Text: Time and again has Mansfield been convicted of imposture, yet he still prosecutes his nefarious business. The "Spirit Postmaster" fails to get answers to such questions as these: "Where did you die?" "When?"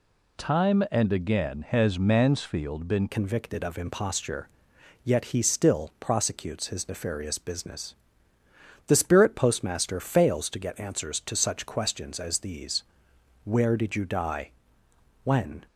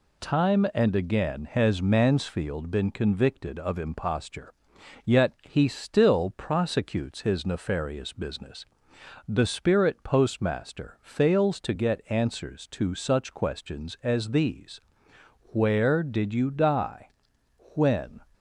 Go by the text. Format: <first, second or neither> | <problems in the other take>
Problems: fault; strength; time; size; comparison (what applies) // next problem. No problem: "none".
second | changes voice at "convicted"; from 3.1 s on; 12.5 s long